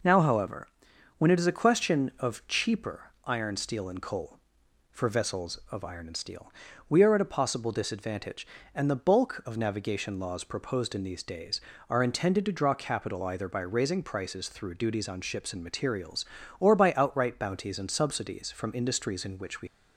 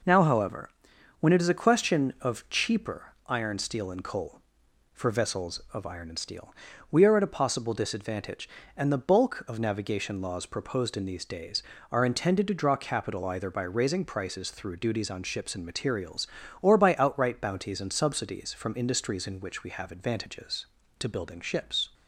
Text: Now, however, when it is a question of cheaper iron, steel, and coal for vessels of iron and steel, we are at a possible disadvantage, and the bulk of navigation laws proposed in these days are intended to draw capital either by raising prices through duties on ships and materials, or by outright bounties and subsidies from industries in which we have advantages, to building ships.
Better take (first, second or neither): second